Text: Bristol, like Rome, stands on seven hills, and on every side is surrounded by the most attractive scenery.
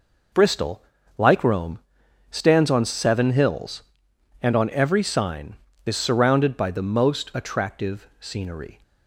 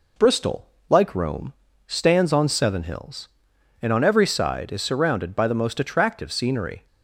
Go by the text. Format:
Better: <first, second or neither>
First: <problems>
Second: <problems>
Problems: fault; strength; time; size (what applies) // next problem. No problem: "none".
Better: second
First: says "sign" for "side"; at 5.0 s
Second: none